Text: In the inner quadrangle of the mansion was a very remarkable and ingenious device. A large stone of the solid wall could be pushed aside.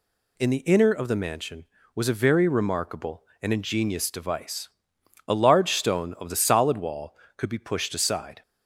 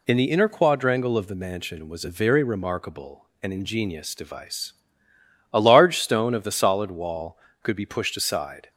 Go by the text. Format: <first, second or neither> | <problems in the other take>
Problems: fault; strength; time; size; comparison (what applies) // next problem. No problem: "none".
second | skips "quadrangle"; at 0.9 s